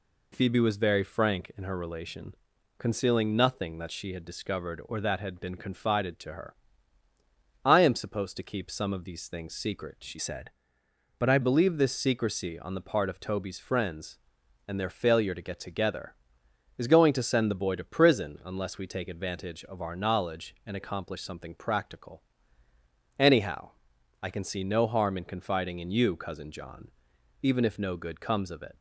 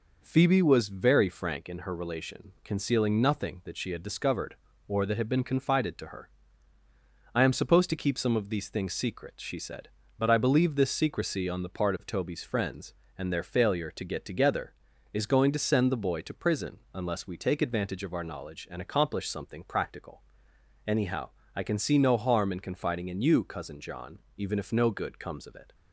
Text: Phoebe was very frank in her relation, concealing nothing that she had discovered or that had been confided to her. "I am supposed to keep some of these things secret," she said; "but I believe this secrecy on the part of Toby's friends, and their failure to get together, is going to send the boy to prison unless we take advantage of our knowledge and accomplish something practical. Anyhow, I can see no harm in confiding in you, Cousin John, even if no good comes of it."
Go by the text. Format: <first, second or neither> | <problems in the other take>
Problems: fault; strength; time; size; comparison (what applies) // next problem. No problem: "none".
second | changes voice from "said" to "I"; from 10.1 to 11.3 s; 1.2 s long